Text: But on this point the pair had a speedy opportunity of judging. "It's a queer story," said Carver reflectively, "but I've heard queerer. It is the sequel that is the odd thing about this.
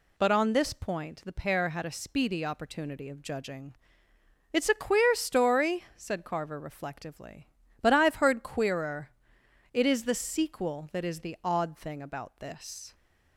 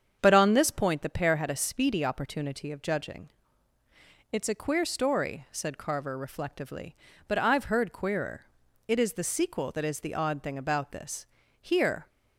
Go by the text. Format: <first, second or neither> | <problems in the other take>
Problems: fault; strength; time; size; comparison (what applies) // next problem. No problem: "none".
first | starts louder than the rest; strong; until 1.2 s; 7.5 dB // goes on to say "Here"; slight; from 11.6 s on; 0.48 s long